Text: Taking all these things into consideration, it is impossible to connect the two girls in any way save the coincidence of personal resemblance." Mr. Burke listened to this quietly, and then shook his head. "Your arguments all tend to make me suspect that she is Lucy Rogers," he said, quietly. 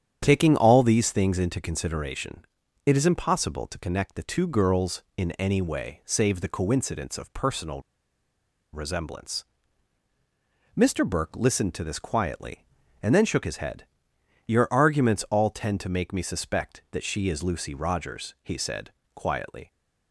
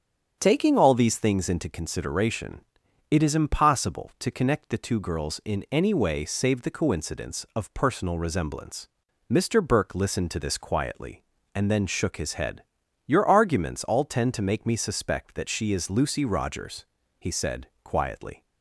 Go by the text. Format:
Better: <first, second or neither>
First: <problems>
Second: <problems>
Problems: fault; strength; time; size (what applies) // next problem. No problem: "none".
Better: second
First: starts louder than the rest; strong; until 1.2 s; 9 dB // pauses between "personal" and "resemblance"; noticeable; at 7.8 s; 0.91 s long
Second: starts louder than the rest; strong; until 1.4 s; 7.5 dB